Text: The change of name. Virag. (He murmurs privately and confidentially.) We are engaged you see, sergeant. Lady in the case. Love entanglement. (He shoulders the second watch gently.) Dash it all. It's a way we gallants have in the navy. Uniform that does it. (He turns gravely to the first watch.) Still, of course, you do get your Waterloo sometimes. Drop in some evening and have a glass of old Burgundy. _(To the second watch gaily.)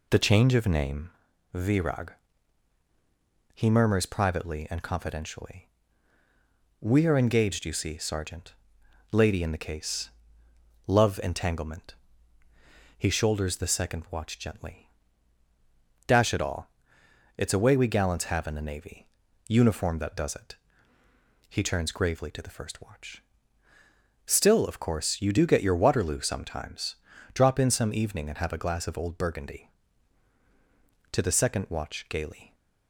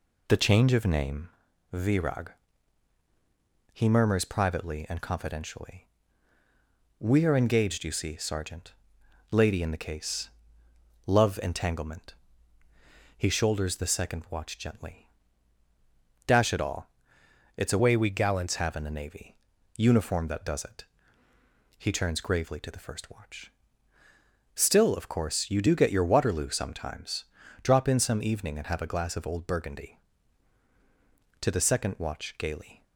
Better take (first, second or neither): first